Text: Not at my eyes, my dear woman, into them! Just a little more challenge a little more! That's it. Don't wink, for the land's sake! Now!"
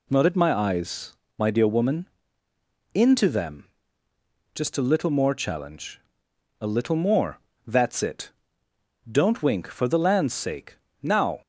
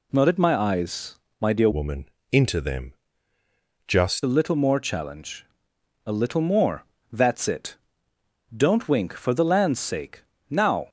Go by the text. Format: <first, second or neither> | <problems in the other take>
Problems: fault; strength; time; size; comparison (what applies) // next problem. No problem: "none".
first | changes voice from "woman" to "Just"; from 1.7 to 4.2 s; 2.5 s long // pauses between "challenge" and "a"; noticeable; at 5.4 s; 0.60 s long; noticeable in the first